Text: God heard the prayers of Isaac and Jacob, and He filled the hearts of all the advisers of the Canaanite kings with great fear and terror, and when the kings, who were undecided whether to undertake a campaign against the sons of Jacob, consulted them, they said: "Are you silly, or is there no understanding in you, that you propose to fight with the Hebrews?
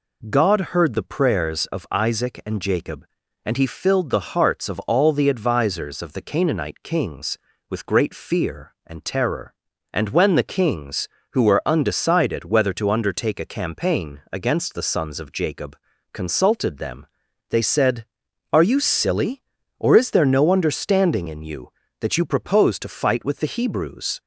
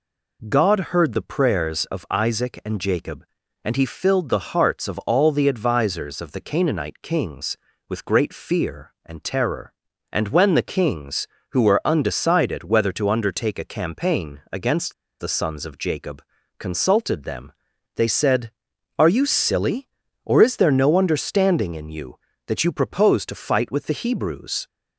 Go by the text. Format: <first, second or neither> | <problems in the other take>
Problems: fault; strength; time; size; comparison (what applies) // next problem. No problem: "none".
first | pauses between "against" and "the"; slight; at 14.9 s; 0.26 s long